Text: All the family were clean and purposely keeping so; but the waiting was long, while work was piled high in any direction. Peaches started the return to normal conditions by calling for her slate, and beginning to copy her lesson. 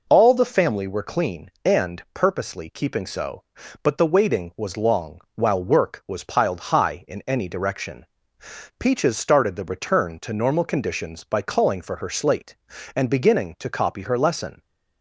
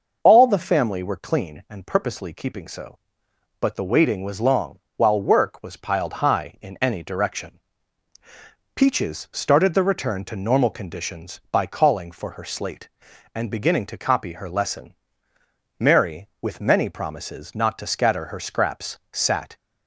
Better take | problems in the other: first | goes on to say "Mary with many promises not to scatter her scraps sat"; strong; from 15.7 s on; 3.7 s long

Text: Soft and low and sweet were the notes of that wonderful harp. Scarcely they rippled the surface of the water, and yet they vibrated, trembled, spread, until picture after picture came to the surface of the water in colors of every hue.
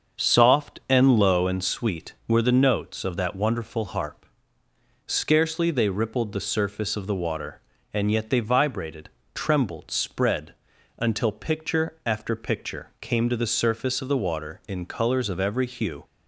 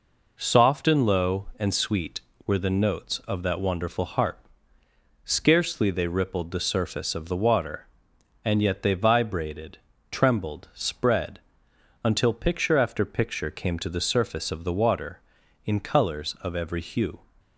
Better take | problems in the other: second | starts louder than the rest; until 1.8 s; 6.5 dB

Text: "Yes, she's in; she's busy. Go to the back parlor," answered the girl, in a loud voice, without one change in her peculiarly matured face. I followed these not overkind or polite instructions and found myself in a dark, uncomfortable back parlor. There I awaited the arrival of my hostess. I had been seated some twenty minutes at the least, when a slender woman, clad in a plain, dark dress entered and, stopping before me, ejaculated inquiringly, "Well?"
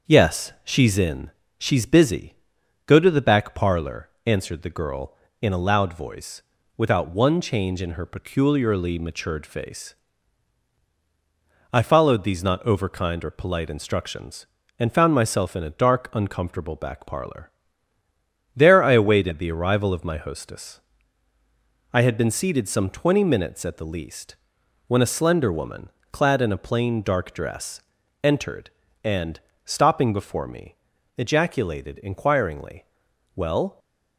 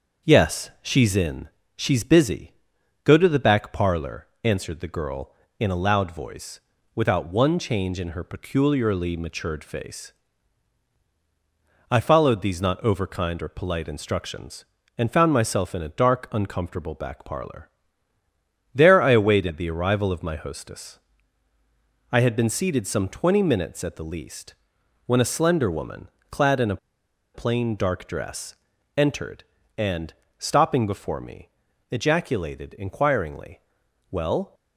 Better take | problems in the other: first | starts louder than the rest; until 1.3 s; 6.5 dB; also in the first // pauses between "a" and "plain"; noticeable; at 26.7 s; 0.57 s long // pauses between "dress" and "entered"; at 28.5 s; 0.42 s long; also in the first

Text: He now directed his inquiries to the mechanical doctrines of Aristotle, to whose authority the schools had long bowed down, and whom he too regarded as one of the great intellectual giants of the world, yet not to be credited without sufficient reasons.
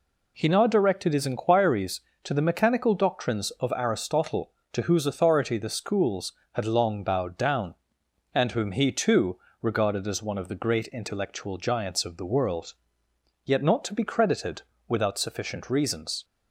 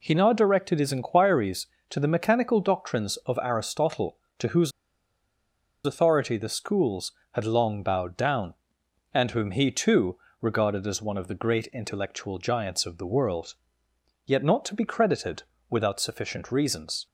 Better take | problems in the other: first | pauses between "whose" and "authority"; at 4.7 s; 1.1 s long // pauses between "too" and "regarded"; slight; at 10.1 s; 0.22 s long; slight in the first // pauses between "credited" and "without"; slight; at 15.4 s; 0.26 s long; slight in the first

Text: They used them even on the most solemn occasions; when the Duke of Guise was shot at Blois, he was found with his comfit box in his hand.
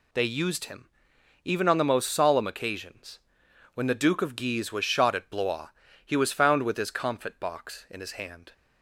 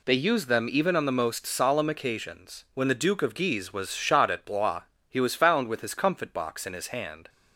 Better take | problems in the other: second | says "him" for "them"; at 0.6 s

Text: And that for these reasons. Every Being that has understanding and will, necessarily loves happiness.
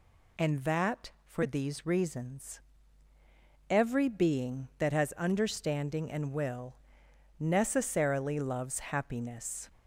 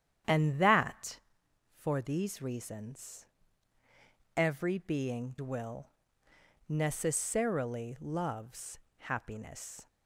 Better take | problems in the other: first | starts louder than the rest; strong; until 1.8 s; 9.5 dB // skips "that has understanding and"; at 5.3 s // pauses between "loves" and "happiness"; slight; at 8.7 s; 0.20 s long

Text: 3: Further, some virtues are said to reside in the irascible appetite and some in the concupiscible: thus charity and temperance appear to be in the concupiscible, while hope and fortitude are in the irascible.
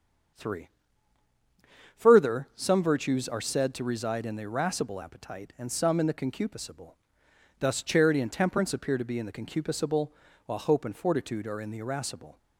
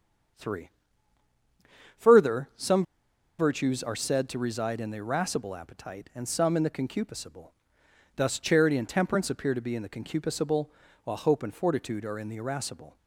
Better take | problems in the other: first | starts louder than the rest; until 2.7 s; 7 dB; also in the first // pauses between "some" and "virtues"; noticeable; at 2.8 s; 0.56 s long

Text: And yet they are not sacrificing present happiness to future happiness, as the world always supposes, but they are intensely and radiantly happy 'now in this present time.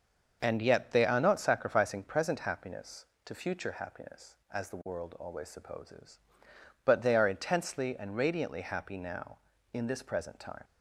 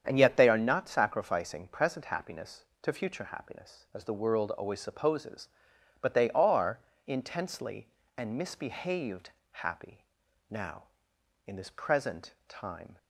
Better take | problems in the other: first | starts louder than the rest; strong; until 1.0 s; 8 dB; also in the first // pauses between "are" and "intensely"; slight; at 6.7 s; 0.30 s long // says "misbehaved" for "radiantly"; at 8.3 s // pauses between "happy" and "now"; noticeable; at 10.0 s; 0.46 s long

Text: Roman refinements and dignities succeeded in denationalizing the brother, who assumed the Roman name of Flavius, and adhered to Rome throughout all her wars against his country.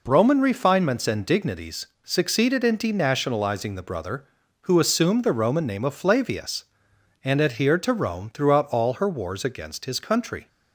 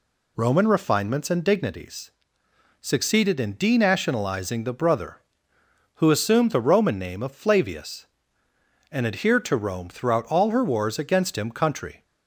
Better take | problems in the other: first | pauses between "dignities" and "succeeded"; noticeable; at 2.1 s; 0.70 s long; slight in the first // says "him" for "his"; at 11.3 s

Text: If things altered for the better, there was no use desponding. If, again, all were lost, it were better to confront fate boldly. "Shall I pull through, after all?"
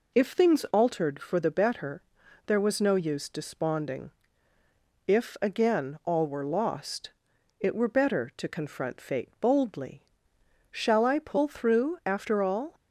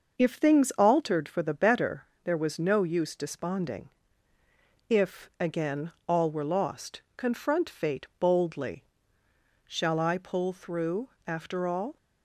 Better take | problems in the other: first | starts louder than the rest; noticeable; until 1.2 s; 6 dB // skips "it were better to"; at 7.0 s

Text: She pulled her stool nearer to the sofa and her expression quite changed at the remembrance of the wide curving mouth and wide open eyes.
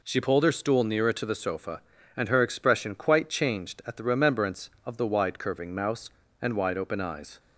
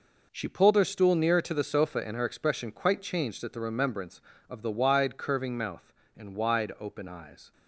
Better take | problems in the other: second | says "mouse" for "mouth"; at 5.7 s

